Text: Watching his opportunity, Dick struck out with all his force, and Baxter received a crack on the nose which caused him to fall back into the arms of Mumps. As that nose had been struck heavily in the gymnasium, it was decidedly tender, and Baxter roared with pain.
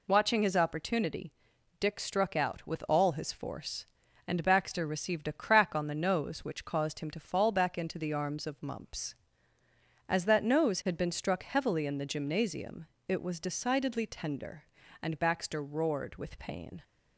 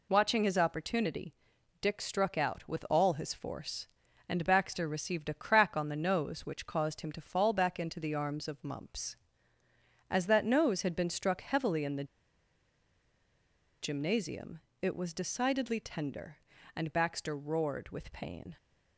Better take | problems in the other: first | pauses between "the" and "gymnasium"; strong; at 12.0 s; 1.7 s long

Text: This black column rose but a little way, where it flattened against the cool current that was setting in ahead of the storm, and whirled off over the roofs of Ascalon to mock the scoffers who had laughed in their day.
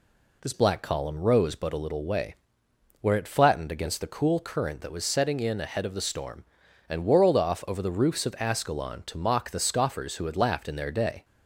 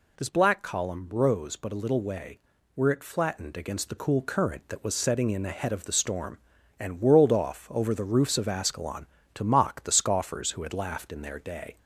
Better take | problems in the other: second | changes voice at "black"; from 0.5 s on; 10.7 s long

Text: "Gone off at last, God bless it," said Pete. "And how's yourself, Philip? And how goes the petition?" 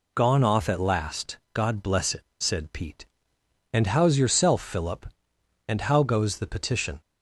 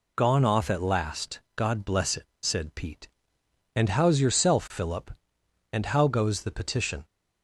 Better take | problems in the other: neither | none

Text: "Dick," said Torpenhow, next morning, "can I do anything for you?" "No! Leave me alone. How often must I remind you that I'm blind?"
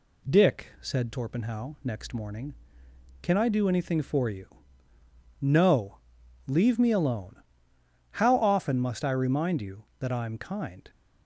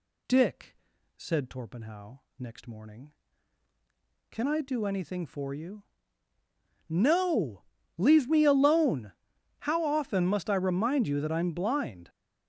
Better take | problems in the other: second | says "kind" for "blind"; at 10.3 s

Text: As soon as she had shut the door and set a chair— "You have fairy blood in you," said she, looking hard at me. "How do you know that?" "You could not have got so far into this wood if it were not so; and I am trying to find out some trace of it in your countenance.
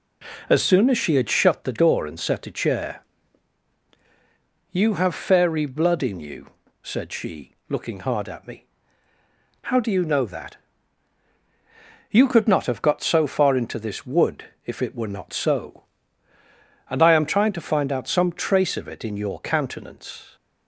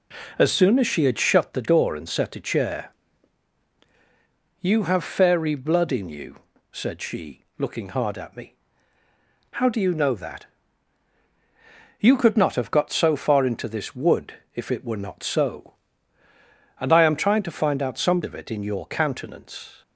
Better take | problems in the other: first | pauses between "wood" and "if"; slight; at 14.3 s; 0.20 s long; slight in the first // skips "trace"; at 18.2 s

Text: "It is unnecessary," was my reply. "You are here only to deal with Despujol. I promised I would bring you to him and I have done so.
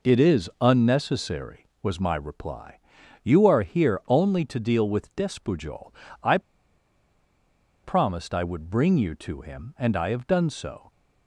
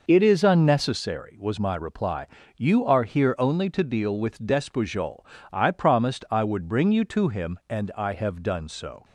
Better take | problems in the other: second | pauses between "I" and "promised"; strong; at 6.3 s; 1.4 s long

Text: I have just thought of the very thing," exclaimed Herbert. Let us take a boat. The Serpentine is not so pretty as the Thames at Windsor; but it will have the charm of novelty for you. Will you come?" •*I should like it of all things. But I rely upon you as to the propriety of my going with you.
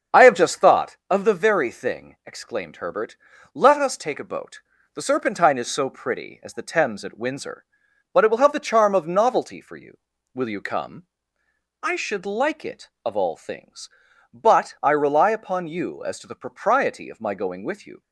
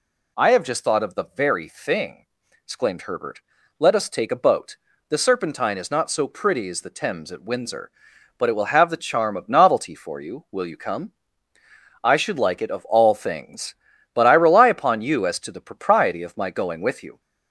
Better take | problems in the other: second | starts louder than the rest; strong; until 1.2 s; 7 dB // skips "not"; at 5.6 s

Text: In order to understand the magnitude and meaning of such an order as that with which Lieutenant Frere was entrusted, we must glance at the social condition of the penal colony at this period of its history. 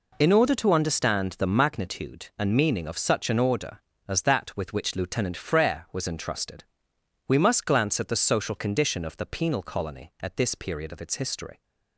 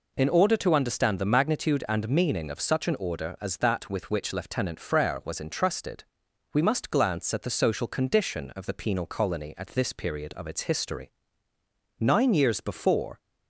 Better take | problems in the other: first | goes on to say "Nine years before"; noticeable; from 11.9 s on; 1.2 s long

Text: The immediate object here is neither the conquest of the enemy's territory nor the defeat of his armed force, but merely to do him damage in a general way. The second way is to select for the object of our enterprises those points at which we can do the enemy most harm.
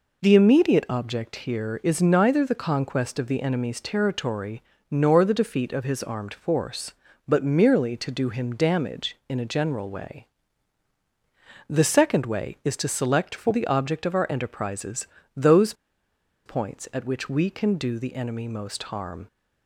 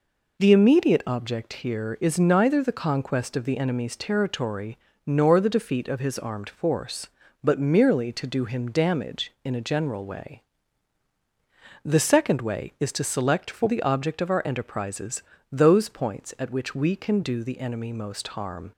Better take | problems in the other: second | pauses between "territory" and "nor"; slight; at 4.6 s; 0.26 s long; slight in the second // pauses between "enterprises" and "those"; slight; at 15.0 s; 0.30 s long; slight in the second // pauses between "those" and "points"; noticeable; at 15.7 s; 0.72 s long

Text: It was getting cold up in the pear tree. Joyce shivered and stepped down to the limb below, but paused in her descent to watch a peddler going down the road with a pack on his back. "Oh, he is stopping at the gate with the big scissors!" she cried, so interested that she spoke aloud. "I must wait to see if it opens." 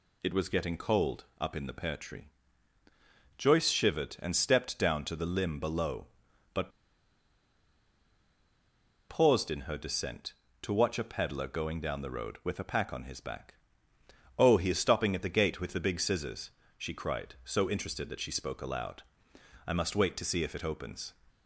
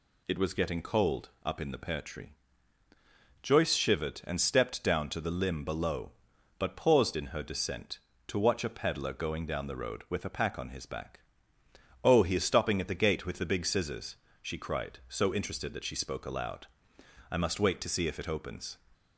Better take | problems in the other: second | pauses between "but" and "paused"; strong; at 6.7 s; 2.3 s long

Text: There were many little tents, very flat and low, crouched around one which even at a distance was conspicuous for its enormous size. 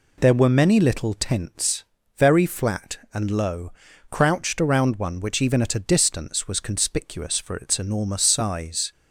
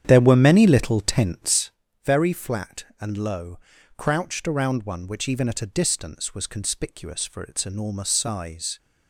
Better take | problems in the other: first | starts louder than the rest; strong; until 1.8 s; 9.5 dB

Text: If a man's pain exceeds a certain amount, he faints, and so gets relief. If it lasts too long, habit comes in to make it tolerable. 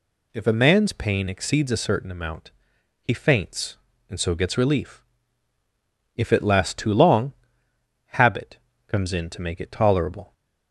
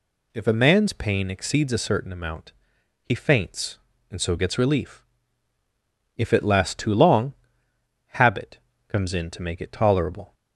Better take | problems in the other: neither | pauses between "habit" and "comes"; slight; the same in both

